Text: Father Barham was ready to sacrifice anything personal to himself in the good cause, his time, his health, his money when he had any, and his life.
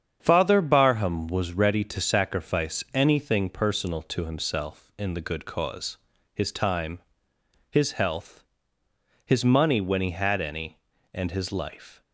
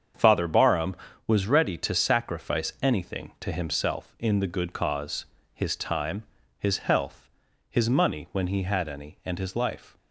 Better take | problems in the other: first | starts louder than the rest; strong; until 1.4 s; 7.5 dB; strong in the first // skips "personal"; at 3.3 s

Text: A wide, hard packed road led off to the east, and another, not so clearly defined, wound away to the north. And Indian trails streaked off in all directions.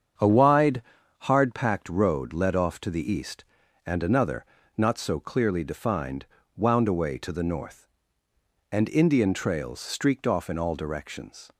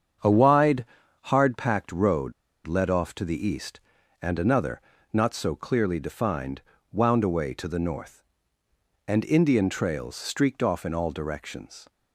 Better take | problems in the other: first | starts louder than the rest; strong; until 1.5 s; 7.5 dB; strong in the first // pauses between "road" and "led"; slight; at 2.3 s; 0.33 s long

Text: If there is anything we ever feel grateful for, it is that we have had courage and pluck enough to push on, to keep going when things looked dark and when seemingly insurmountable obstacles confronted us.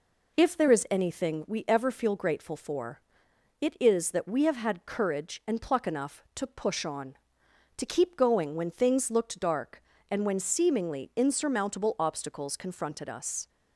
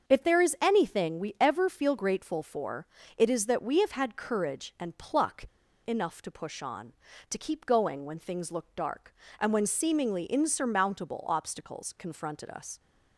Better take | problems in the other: first | starts louder than the rest; until 1.1 s; 6.5 dB // pauses between "pluck" and "enough"; at 5.4 s; 0.39 s long

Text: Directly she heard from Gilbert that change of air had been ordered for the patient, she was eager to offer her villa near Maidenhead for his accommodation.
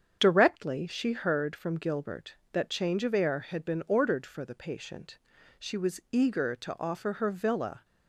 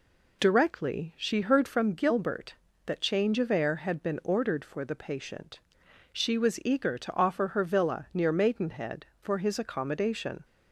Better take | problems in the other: second | starts louder than the rest; strong; until 1.2 s; 7.5 dB // stops before "near Maidenhead for his accommodation"; at 7.8 s

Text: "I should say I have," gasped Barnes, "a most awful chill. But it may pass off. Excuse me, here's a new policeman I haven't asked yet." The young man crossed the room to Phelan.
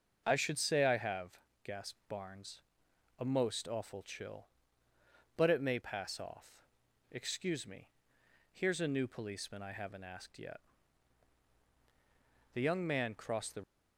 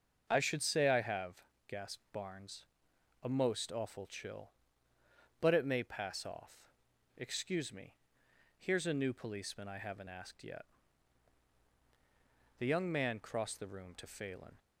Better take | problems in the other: second | starts louder than the rest; until 1.2 s; 6.5 dB; also in the second // stops before "room to Phelan"; at 13.6 s

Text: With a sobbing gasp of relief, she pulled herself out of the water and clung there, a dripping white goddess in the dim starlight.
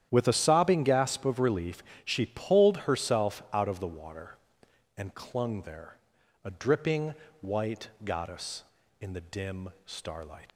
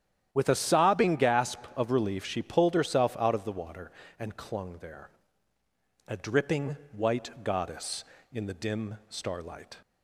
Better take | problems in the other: second | starts louder than the rest; strong; until 1.1 s; 10.5 dB; strong in the second // pauses between "dripping" and "white"; slight; at 7.1 s; 0.26 s long // pauses between "white" and "goddess"; slight; at 7.8 s; 0.16 s long // pauses between "dim" and "starlight"; slight; at 9.7 s; 0.16 s long // leaves "starlight" unfinished; at 10.4 s; 75 ms

